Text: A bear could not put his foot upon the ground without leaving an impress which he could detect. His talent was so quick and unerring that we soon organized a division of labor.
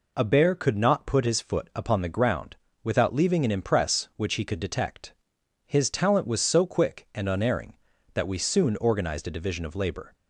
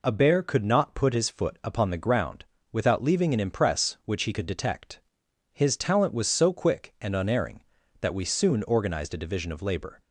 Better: neither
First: pauses between "ground" and "without"; slight; at 2.5 s; 0.26 s long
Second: pauses between "ground" and "without"; slight; at 2.4 s; 0.26 s long

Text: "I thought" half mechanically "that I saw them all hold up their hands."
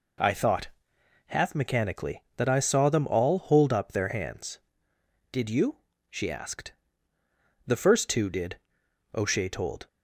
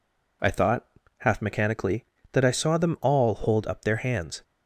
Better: second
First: pauses between "thought" and "half"; noticeable; at 0.6 s; 0.60 s long // goes on to say "Did you she asked The first two did O'Shea told"; strong; from 5.3 s on; 4.5 s long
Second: pauses between "thought" and "half"; slight; at 0.8 s; 0.32 s long

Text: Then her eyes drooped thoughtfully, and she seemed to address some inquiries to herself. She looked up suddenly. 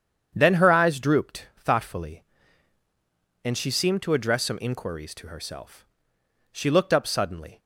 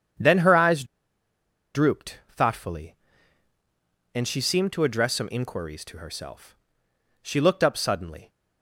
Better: first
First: starts louder than the rest; strong; until 1.3 s; 8 dB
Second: starts louder than the rest; strong; until 2.1 s; 8 dB // pauses between "eyes" and "drooped"; noticeable; at 0.8 s; 0.90 s long

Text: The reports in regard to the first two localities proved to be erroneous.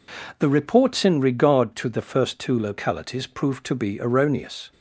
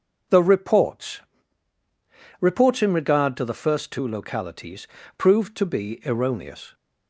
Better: first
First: none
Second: says "reports" twice; at 2.3 s // pauses between "localities" and "proved"; slight; at 4.8 s; 0.30 s long

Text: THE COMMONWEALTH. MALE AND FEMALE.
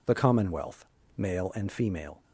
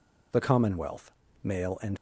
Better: first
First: none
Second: stops before "FEMALE"; at 1.9 s

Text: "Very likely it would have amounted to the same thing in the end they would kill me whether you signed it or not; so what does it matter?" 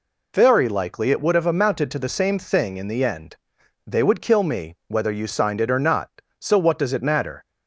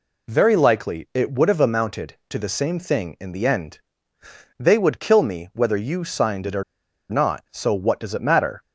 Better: first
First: pauses between "end" and "they"; noticeable; at 3.3 s; 0.52 s long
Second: pauses between "end" and "they"; noticeable; at 3.8 s; 0.76 s long // pauses between "or" and "not"; noticeable; at 6.6 s; 0.46 s long

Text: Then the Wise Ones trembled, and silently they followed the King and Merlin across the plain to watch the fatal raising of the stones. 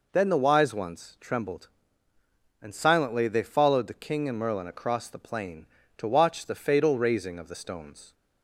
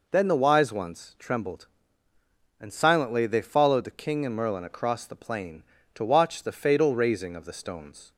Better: neither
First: none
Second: none

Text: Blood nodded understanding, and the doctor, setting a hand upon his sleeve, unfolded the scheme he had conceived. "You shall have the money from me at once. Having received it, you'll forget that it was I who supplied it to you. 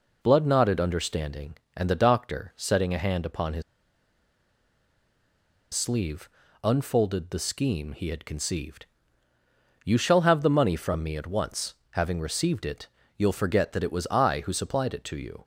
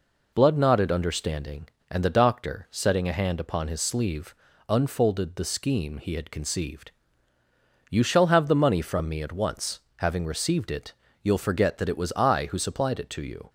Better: second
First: pauses between "his" and "sleeve"; strong; at 3.6 s; 2.1 s long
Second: none

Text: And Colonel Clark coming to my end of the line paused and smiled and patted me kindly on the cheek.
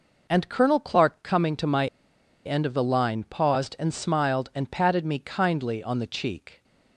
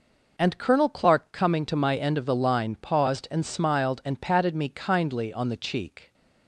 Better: second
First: pauses between "my" and "end"; noticeable; at 1.8 s; 0.59 s long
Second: none

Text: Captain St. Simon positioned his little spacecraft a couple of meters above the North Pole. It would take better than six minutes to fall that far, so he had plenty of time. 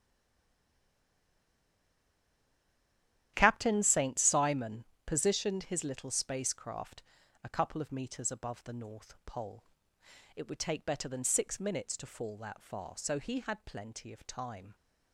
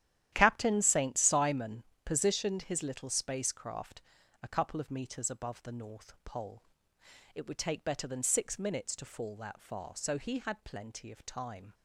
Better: second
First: stays silent before the first word; strong; until 3.3 s; 3.3 s long // starts louder than the rest; strong; until 4.3 s; 11.5 dB // pauses between "Simon" and "positioned"; slight; at 4.8 s; 0.22 s long // pauses between "spacecraft" and "a"; at 7.0 s; 0.40 s long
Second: starts louder than the rest; strong; until 1.3 s; 11.5 dB // pauses between "Simon" and "positioned"; slight; at 1.8 s; 0.22 s long // pauses between "spacecraft" and "a"; at 4.0 s; 0.40 s long

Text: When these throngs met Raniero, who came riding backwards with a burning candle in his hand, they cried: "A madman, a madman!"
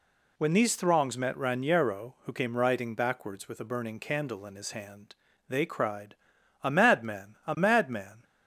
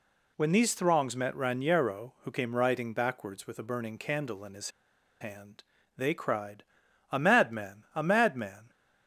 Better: first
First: none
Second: pauses between "his" and "hand"; noticeable; at 4.7 s; 0.50 s long

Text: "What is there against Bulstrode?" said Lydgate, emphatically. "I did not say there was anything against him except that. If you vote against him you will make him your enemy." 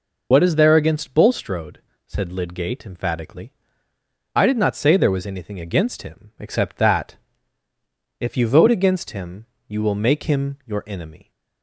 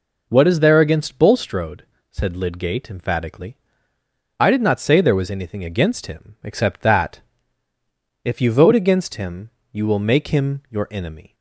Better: second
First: loses the start of "What"; at 0.3 s; 65 ms // pauses between "him" and "you"; slight; at 9.4 s; 0.24 s long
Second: pauses between "him" and "you"; slight; at 9.4 s; 0.24 s long

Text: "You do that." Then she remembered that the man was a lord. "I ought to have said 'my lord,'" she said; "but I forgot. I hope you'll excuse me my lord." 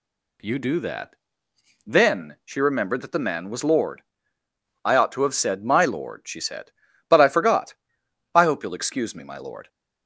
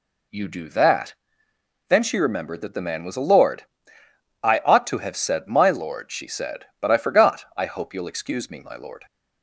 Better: second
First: skips "a"; at 3.6 s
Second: none

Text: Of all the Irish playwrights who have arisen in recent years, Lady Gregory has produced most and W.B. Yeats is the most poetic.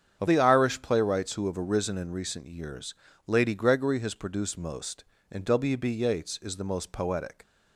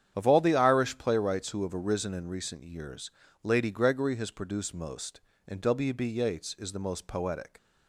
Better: second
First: starts louder than the rest; strong; until 1.2 s; 8 dB // skips "all"; at 0.2 s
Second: starts louder than the rest; strong; until 1.1 s; 9 dB

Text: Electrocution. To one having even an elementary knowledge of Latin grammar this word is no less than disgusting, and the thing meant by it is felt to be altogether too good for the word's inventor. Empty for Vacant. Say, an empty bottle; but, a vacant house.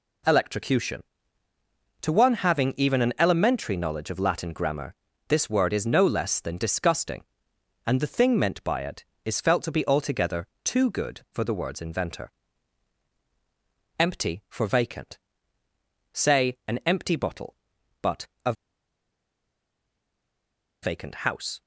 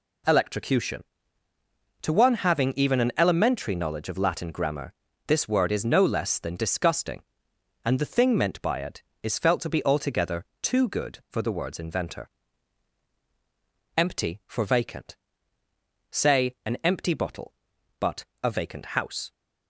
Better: second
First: pauses between "grammar" and "this"; slight; at 4.9 s; 0.34 s long // pauses between "altogether" and "too"; slight; at 10.4 s; 0.16 s long // pauses between "a" and "vacant"; strong; at 18.5 s; 2.3 s long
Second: pauses between "grammar" and "this"; slight; at 4.9 s; 0.34 s long // pauses between "altogether" and "too"; slight; at 10.4 s; 0.16 s long

